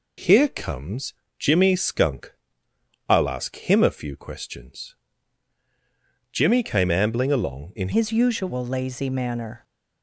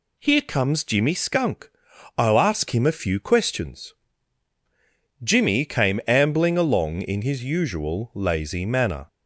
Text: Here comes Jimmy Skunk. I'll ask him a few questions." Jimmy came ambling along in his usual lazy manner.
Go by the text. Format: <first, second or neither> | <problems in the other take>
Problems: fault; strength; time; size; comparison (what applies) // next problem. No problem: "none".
second | pauses between "comes" and "Jimmy"; slight; at 1.1 s; 0.26 s long // changes voice at "his"; from 7.9 s on; 1.7 s long